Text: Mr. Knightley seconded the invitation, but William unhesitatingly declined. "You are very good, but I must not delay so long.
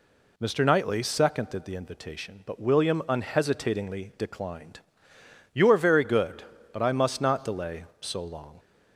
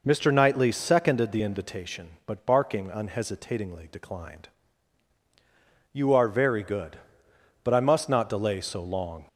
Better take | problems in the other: first | says "Barking" for "William"; at 2.4 s

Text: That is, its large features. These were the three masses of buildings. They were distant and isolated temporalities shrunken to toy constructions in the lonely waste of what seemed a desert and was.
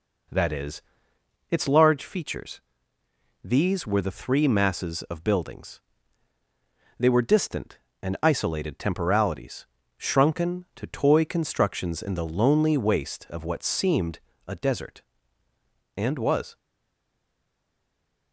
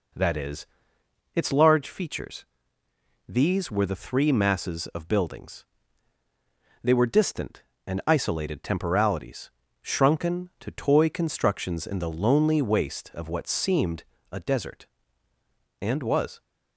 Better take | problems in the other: second | pauses between "temporalities" and "shrunken"; slight; at 9.6 s; 0.34 s long; slight in the second // pauses between "seemed" and "a"; slight; at 14.1 s; 0.26 s long; slight in the second // stays silent after the last word; noticeable; from 16.5 s on; 1.8 s long

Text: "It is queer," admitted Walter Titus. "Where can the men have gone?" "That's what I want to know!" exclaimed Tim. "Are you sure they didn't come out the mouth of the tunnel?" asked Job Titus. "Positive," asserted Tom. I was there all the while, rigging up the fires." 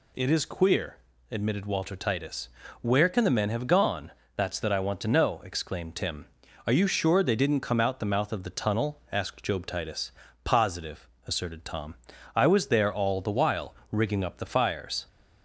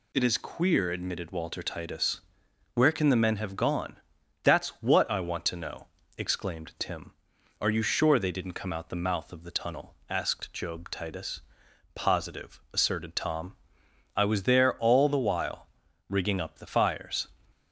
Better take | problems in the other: second | says "that" for "what"; at 4.5 s

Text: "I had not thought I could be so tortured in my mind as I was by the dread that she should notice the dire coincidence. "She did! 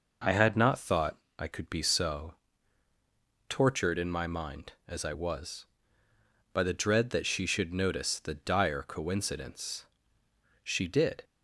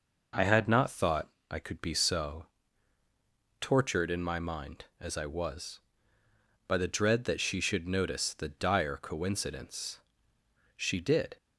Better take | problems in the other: neither | pauses between "thought" and "I"; slight; the same in both // pauses between "so" and "tortured"; the same in both

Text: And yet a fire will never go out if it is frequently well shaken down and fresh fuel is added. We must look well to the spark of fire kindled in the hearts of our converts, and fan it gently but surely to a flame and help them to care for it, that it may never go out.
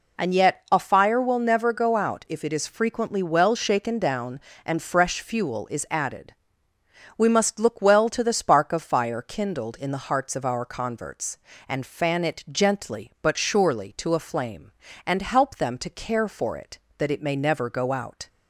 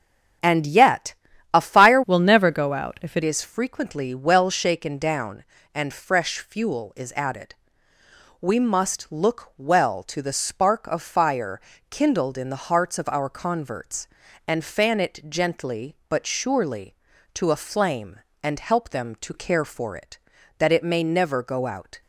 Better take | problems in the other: first | starts louder than the rest; strong; until 1.8 s; 8 dB // pauses between "yet" and "a"; at 1.1 s; 0.40 s long // changes voice from "will" to "it"; from 2.0 to 3.2 s; 1.2 s long // pauses between "fire" and "kindled"; slight; at 11.6 s; 0.30 s long

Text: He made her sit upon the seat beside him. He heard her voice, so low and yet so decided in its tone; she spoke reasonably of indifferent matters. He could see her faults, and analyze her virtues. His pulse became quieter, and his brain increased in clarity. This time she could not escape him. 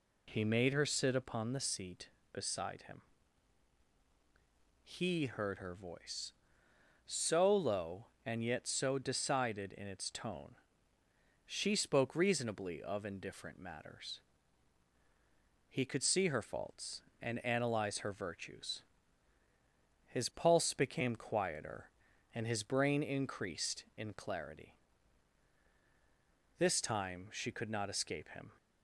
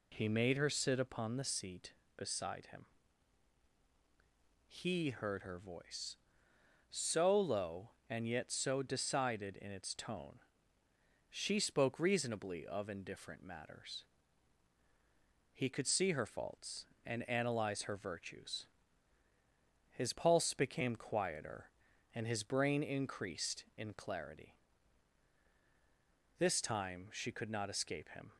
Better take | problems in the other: neither | none

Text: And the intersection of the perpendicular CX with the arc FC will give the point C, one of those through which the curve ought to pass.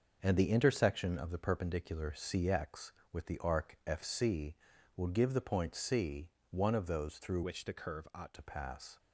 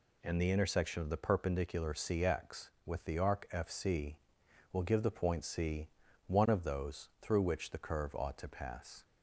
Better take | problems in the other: second | changes voice from "which" to "ought"; from 7.4 to 8.3 s; 0.9 s long

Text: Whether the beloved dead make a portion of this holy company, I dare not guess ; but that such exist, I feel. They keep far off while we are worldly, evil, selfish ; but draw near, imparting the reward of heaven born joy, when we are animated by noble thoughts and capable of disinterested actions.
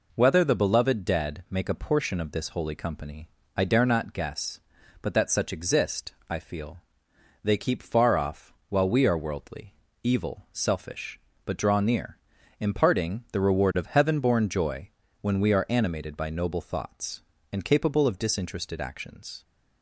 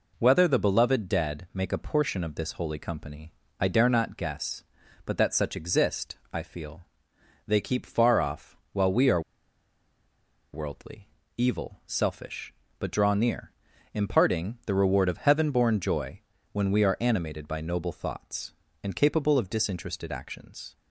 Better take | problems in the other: first | pauses between "are" and "worldly"; strong; at 9.2 s; 1.3 s long

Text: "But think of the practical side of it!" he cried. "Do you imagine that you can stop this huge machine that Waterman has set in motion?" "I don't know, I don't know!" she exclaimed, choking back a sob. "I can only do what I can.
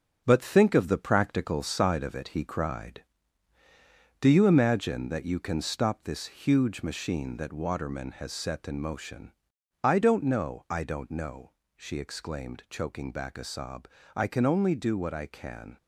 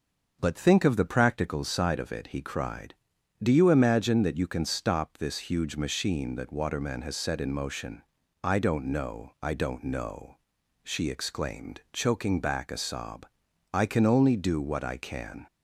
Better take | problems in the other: second | gets quieter; noticeable; throughout; 6 dB // starts louder than the rest; until 1.2 s; 7 dB; also in the second

